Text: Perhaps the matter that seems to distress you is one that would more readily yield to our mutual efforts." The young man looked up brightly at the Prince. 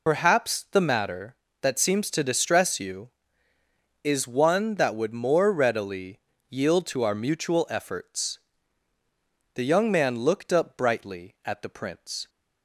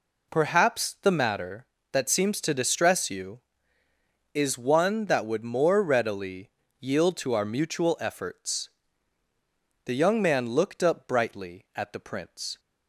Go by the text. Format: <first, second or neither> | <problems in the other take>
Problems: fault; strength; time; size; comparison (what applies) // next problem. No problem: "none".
second | loses the start of "Perhaps"; at 0.0 s; 75 ms // pauses between "readily" and "yield"; slight; at 6.2 s; 0.28 s long; slight in the second